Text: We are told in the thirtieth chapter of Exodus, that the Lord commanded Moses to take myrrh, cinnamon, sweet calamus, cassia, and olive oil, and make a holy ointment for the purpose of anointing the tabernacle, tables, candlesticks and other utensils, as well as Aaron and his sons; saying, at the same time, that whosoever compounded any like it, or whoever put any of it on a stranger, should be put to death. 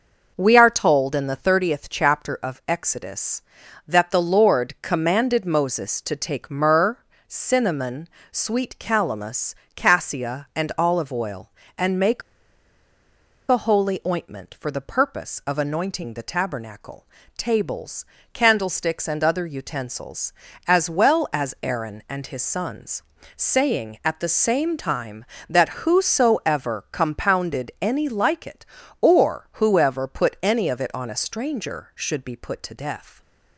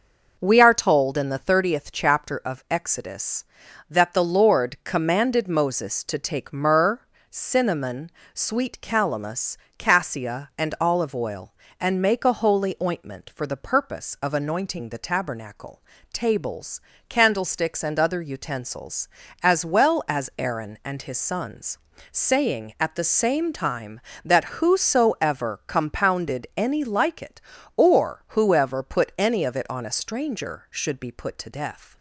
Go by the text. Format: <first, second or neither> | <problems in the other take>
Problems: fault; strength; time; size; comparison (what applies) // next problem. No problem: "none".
second | pauses between "make" and "a"; strong; at 12.2 s; 1.2 s long